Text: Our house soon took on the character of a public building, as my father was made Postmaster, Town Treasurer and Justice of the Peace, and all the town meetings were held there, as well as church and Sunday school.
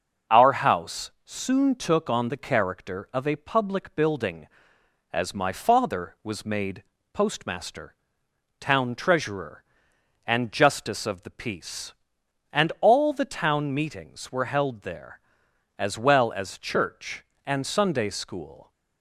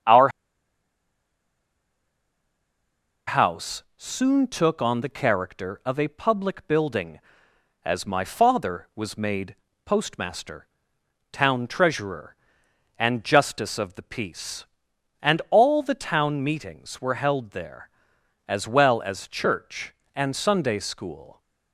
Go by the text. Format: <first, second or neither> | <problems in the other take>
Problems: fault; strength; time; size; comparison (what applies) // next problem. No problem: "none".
first | pauses between "Our" and "house"; strong; at 0.2 s; 2.9 s long // pauses between "made" and "Postmaster"; slight; at 9.5 s; 0.30 s long; slight in the first